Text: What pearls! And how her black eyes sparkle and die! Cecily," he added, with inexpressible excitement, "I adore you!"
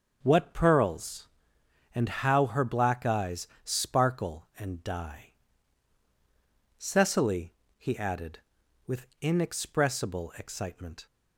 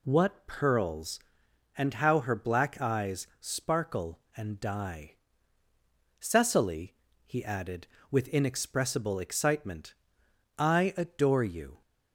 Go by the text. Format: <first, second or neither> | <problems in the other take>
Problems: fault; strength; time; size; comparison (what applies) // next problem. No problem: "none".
second | starts louder than the rest; until 1.2 s; 6.5 dB // pauses between "eyes" and "sparkle"; slight; at 3.4 s; 0.18 s long // pauses between "with" and "inexpressible"; slight; at 9.0 s; 0.16 s long // stops before "I adore you"; at 11.0 s